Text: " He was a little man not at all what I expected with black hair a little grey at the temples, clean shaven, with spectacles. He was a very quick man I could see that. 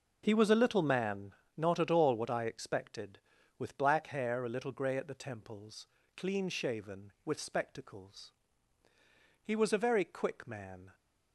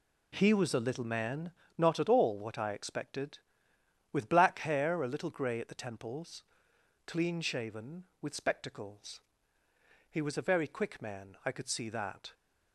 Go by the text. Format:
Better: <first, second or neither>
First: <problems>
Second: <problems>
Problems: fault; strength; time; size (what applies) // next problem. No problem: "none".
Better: second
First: pauses between "man" and "not"; slight; at 1.3 s; 0.20 s long // stops before "I could see that"; at 10.9 s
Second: pauses between "man" and "not"; slight; at 1.5 s; 0.26 s long